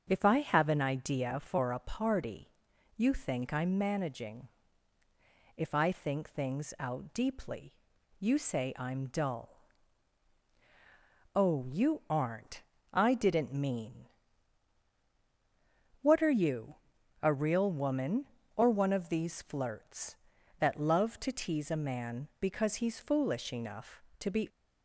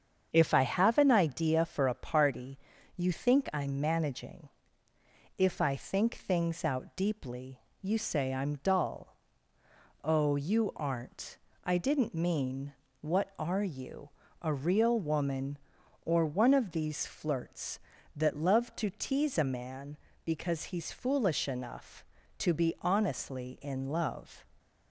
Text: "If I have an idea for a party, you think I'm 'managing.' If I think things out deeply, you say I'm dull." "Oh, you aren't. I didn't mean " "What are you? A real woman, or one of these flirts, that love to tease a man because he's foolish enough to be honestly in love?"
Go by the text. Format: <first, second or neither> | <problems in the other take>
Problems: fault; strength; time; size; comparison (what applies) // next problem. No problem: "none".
second | starts louder than the rest; until 1.1 s; 7 dB; strong in the second // stops before "honestly in love"; at 24.4 s